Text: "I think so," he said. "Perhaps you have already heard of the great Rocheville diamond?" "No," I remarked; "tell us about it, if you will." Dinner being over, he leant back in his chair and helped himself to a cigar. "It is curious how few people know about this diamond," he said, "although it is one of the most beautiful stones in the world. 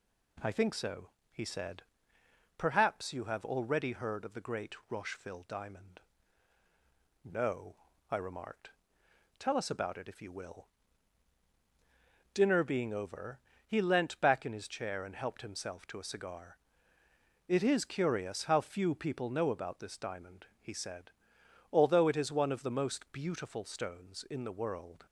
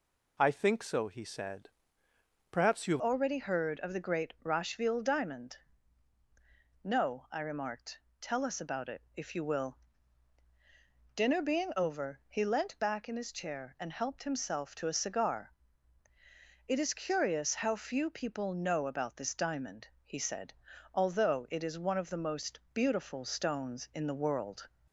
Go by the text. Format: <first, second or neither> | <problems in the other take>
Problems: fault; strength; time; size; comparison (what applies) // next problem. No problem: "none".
first | changes voice at "already"; from 2.9 s on; 21.7 s long